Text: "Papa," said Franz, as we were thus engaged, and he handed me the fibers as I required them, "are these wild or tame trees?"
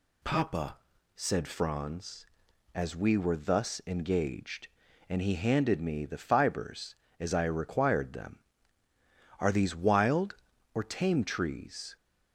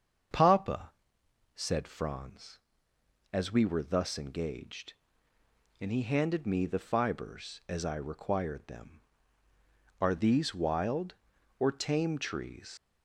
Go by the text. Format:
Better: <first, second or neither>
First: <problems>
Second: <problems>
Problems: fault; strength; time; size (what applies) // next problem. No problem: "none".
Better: first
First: none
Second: starts louder than the rest; until 1.9 s; 7 dB // leaves "trees" unfinished; at 12.7 s; 90 ms